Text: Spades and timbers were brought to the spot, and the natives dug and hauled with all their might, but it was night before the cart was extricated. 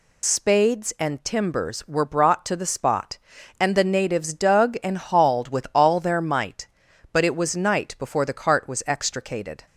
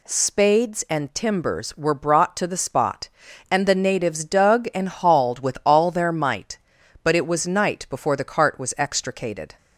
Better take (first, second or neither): second